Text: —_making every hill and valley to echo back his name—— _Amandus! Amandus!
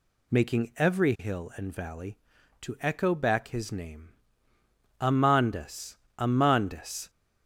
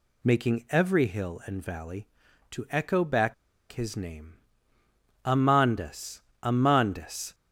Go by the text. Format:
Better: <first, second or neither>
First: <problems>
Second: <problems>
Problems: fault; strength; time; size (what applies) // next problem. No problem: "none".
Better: first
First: none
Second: pauses between "back" and "his"; at 3.3 s; 0.37 s long